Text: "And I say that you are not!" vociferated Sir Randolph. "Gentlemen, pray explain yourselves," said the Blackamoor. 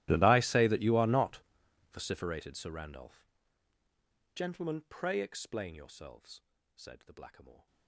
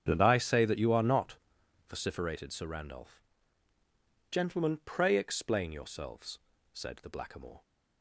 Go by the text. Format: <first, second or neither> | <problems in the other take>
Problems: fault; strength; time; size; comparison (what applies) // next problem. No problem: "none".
second | gets quieter; strong; throughout; 25.5 dB // starts louder than the rest; strong; until 1.1 s; 15 dB; strong in the second